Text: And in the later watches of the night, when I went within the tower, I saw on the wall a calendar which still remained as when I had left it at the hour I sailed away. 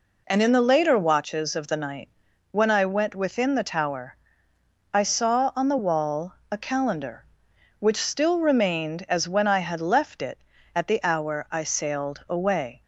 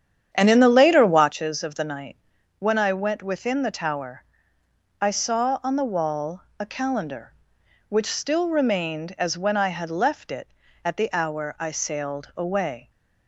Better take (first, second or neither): first